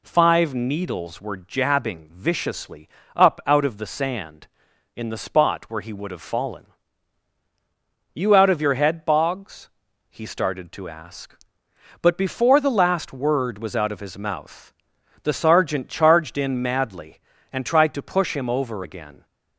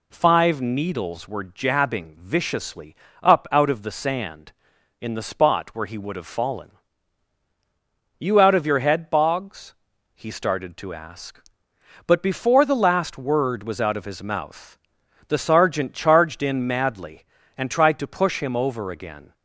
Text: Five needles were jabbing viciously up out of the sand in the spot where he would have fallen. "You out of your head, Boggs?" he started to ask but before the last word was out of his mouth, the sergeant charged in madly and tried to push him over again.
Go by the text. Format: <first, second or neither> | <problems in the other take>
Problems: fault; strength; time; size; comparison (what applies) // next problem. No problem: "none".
neither | pauses between "viciously" and "up"; slight; the same in both